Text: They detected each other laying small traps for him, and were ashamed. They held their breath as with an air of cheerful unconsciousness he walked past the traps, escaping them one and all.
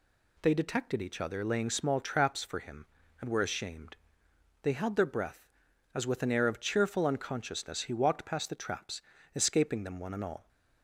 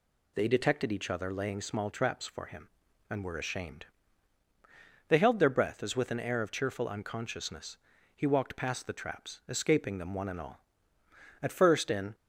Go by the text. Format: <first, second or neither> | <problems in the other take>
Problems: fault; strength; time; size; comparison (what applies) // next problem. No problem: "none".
first | pauses between "unconsciousness" and "he"; at 7.7 s; 0.40 s long // goes on to say "At first in"; noticeable; from 11.4 s on; 0.72 s long